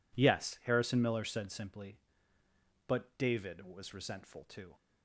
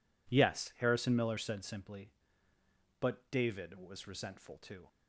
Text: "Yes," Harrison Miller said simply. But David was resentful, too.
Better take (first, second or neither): neither